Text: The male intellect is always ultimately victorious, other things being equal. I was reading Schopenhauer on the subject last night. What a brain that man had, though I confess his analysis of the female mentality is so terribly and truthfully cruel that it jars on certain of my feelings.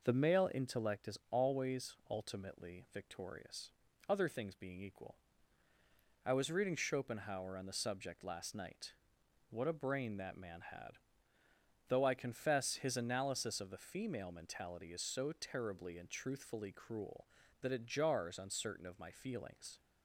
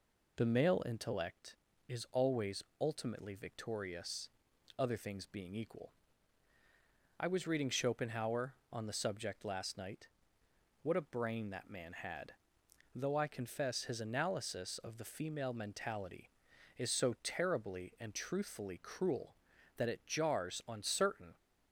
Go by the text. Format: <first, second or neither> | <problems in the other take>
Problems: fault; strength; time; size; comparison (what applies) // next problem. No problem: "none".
first | pauses between "always" and "ultimately"; slight; at 2.6 s; 0.16 s long // stops before "of my feelings"; at 21.3 s